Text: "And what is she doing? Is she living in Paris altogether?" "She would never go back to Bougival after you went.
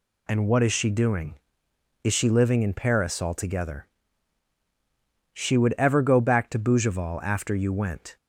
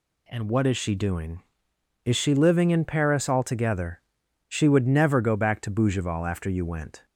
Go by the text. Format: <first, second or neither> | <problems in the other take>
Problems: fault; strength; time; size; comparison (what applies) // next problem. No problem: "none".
second | says "ever" for "never"; at 5.7 s